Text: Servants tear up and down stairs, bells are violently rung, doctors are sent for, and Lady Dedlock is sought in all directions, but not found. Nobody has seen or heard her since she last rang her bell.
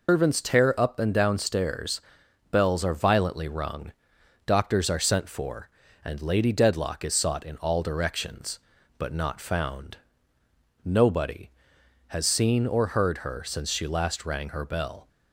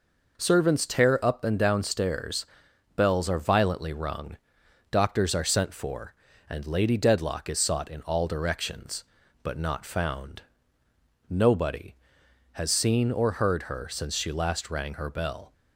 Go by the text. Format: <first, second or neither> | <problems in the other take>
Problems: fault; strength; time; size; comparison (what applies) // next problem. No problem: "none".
second | loses the start of "Servants"; at 0.0 s; 165 ms